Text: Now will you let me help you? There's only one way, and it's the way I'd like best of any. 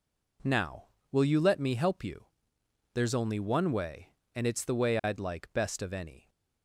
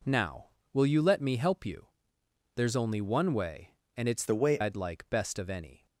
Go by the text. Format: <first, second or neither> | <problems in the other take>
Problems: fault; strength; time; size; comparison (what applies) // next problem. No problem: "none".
first | changes voice from "the" to "way"; from 4.2 to 4.6 s; 0.4 s long